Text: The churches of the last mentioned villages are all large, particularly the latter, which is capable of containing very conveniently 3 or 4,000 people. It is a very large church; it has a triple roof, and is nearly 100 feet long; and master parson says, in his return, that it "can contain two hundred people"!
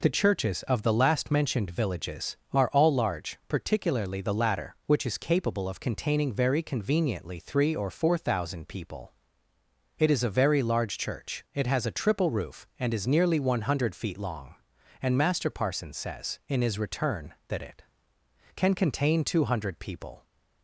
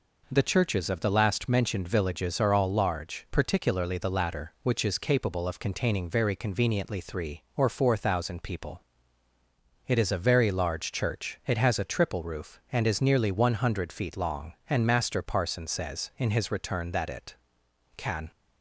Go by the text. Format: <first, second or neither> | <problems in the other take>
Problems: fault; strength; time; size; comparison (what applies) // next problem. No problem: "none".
first | stops before "contain two hundred people"; at 18.3 s